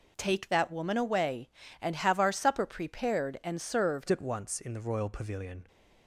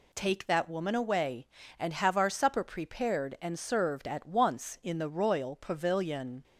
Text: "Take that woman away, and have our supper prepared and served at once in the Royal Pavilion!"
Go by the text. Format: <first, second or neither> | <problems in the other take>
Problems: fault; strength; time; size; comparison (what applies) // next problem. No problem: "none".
second | changes voice at "at"; from 4.0 s on; 1.6 s long